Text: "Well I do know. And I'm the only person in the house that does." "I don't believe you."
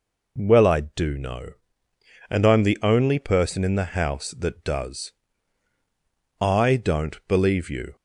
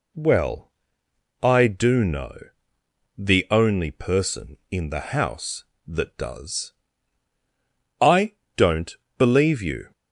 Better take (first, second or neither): first